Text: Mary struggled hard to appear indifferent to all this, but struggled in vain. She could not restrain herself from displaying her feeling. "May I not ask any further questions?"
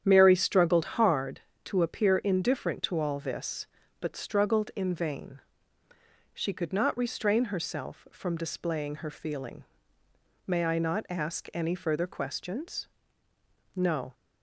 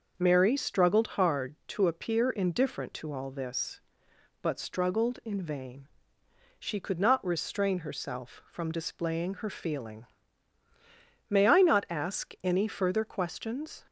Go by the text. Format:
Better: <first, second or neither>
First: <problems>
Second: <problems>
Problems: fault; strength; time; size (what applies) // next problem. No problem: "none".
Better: second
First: starts louder than the rest; strong; until 1.0 s; 9 dB // goes on to say "No"; slight; from 13.7 s on; 0.40 s long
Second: none